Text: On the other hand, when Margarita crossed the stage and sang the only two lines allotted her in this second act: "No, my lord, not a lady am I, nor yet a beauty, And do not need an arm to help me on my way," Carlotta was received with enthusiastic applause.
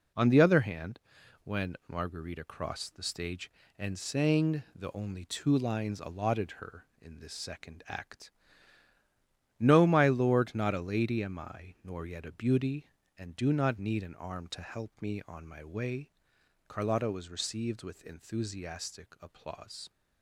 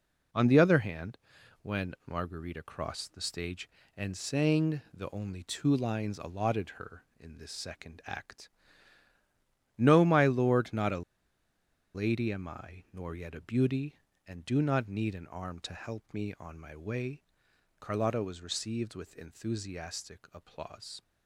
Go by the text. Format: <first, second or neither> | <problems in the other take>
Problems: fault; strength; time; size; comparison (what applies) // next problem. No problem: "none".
first | pauses between "a" and "lady"; noticeable; at 11.0 s; 0.93 s long